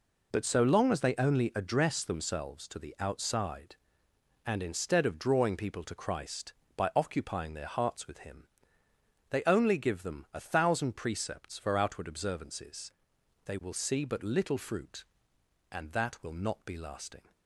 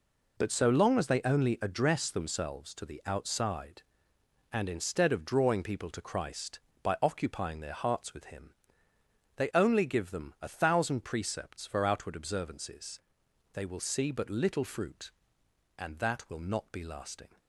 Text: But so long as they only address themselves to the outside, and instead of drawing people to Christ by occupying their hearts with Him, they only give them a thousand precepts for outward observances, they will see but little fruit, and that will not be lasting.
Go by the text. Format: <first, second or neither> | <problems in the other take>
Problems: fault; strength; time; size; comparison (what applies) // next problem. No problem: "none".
neither | none